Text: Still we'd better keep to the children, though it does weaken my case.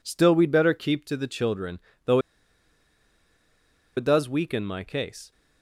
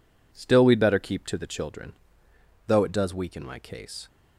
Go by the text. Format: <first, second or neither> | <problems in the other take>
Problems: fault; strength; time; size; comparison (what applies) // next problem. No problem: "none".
second | pauses between "though" and "it"; strong; at 2.1 s; 1.7 s long